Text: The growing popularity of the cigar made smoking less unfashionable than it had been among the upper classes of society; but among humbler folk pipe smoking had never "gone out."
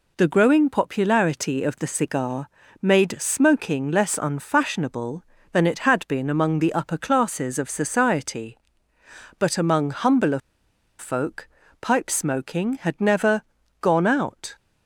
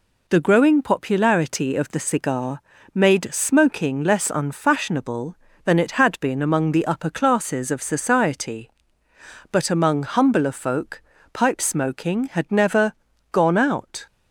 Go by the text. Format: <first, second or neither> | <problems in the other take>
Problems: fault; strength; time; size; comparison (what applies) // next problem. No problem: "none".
second | pauses between "cigar" and "made"; slight; at 2.4 s; 0.32 s long; slight in the second // pauses between "humbler" and "folk"; noticeable; at 10.3 s; 0.60 s long // pauses between "folk" and "pipe"; slight; at 11.4 s; 0.32 s long; slight in the second // pauses between "never" and "gone"; at 13.4 s; 0.38 s long; also in the second